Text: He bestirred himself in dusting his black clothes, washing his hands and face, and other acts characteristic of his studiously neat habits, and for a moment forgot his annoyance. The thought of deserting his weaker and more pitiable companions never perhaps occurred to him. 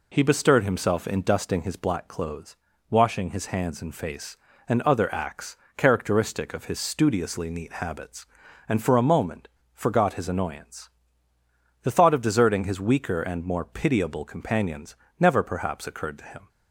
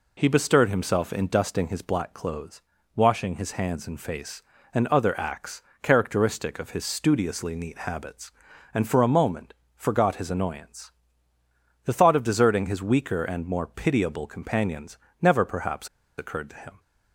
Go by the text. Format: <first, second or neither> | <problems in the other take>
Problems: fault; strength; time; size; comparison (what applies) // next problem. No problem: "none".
first | pauses between "acts" and "characteristic"; slight; at 5.6 s; 0.18 s long; slight in the first // pauses between "moment" and "forgot"; slight; at 9.5 s; 0.22 s long; slight in the first // pauses between "companions" and "never"; slight; at 14.9 s; 0.24 s long; slight in the first // pauses between "perhaps" and "occurred"; slight; at 15.8 s; 0.29 s long